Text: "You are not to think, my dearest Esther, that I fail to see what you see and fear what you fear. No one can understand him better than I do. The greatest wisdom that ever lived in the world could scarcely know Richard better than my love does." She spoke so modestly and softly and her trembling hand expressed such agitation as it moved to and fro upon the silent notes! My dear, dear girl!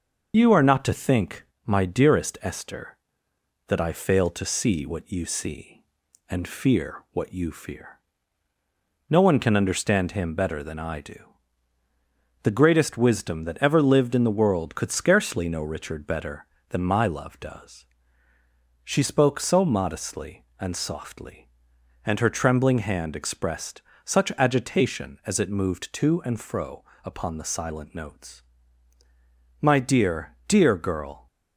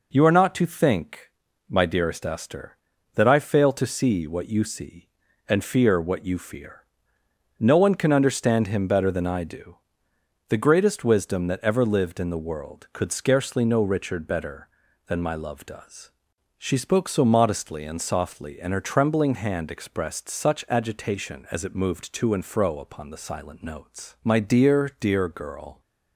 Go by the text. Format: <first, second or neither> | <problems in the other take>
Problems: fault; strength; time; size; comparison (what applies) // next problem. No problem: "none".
second | loses the start of "You"; at 0.3 s; 40 ms // starts louder than the rest; noticeable; until 1.3 s; 6 dB // pauses between "expressed" and "such"; slight; at 23.8 s; 0.22 s long // pauses between "fro" and "upon"; slight; at 26.8 s; 0.22 s long